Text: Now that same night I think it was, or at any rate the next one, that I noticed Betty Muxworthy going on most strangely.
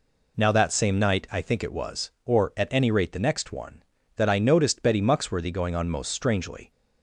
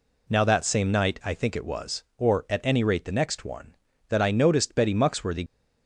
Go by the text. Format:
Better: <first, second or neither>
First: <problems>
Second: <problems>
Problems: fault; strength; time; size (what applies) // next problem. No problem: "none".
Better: first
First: none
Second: stops before "going on most strangely"; at 5.4 s